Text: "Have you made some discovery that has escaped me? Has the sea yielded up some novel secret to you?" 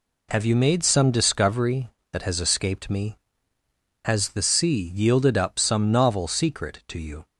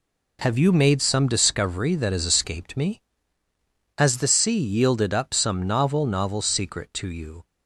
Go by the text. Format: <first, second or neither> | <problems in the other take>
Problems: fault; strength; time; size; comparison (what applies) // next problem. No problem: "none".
first | says "novel" twice; at 6.0 s